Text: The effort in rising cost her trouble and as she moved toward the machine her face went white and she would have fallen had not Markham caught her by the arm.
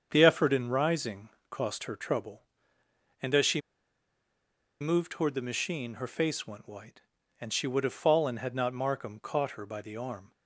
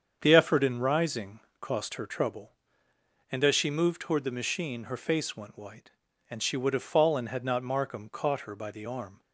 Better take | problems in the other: second | starts louder than the rest; strong; until 1.1 s; 7.5 dB; strong in the second // pauses between "rising" and "cost"; slight; at 1.2 s; 0.22 s long; slight in the second // pauses between "she" and "moved"; at 3.5 s; 1.2 s long

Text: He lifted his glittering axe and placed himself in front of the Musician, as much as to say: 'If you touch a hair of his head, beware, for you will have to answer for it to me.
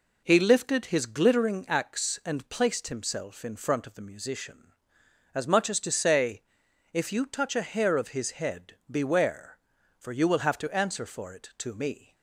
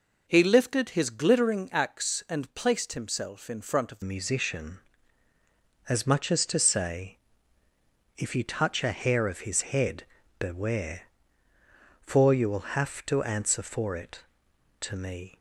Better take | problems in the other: first | changes voice at "Musician"; from 4.0 s on; 11.3 s long

